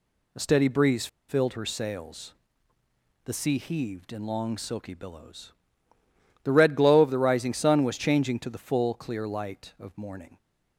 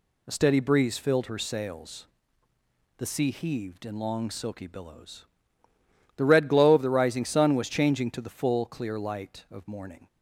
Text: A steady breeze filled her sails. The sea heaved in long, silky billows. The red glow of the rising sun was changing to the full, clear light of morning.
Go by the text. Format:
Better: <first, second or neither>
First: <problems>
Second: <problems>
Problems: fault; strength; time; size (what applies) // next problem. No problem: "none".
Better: second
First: pauses between "breeze" and "filled"; slight; at 1.0 s; 0.21 s long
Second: none